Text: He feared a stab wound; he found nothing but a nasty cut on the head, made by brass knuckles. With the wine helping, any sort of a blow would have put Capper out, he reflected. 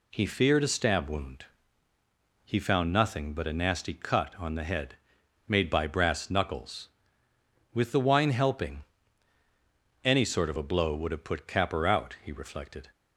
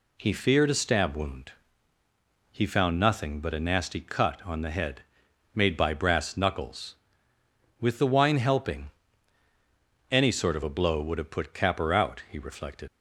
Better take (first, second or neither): first